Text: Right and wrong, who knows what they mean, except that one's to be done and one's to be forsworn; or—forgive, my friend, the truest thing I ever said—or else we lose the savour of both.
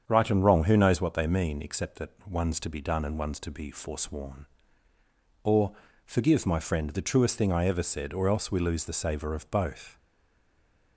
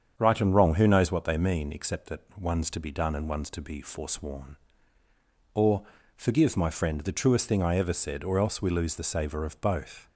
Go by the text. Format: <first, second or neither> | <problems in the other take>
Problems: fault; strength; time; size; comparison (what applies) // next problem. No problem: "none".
second | starts louder than the rest; strong; until 1.0 s; 7.5 dB; strong in the second // pauses between "that" and "one's"; slight; at 2.1 s; 0.18 s long; slight in the second // stays silent after the last word; from 9.9 s on; 1.0 s long